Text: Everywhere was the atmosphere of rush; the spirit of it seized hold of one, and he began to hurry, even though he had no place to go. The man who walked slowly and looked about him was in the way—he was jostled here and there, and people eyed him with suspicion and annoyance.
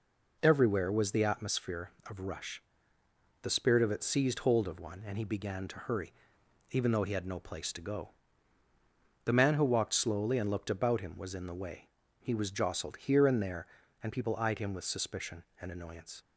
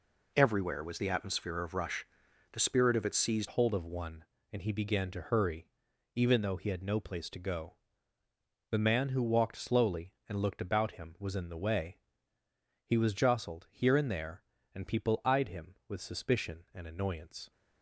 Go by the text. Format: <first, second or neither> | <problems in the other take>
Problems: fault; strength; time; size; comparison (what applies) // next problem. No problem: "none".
first | changes voice at "hold"; from 3.4 s on; 14.1 s long